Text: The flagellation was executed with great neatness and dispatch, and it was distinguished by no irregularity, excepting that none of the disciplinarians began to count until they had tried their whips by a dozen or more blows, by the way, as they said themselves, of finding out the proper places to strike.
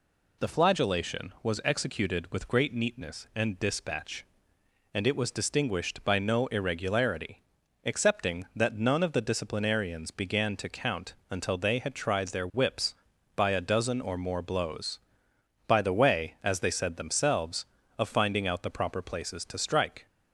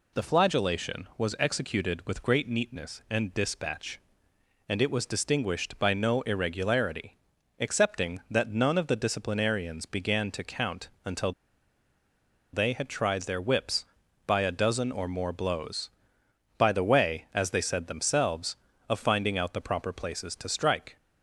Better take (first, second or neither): first